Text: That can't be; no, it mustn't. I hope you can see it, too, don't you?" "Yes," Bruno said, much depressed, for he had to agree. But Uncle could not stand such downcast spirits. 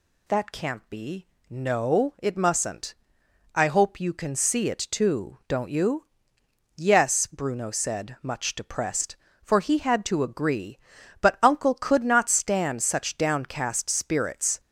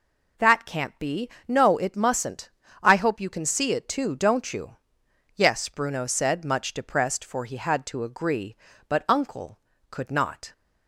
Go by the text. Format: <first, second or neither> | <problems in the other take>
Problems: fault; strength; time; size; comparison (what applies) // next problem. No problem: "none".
first | stops before "stand such downcast spirits"; at 10.5 s